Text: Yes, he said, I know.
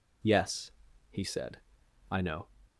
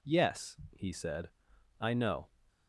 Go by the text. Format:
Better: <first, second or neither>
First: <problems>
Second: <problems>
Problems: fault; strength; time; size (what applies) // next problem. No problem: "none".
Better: neither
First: none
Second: none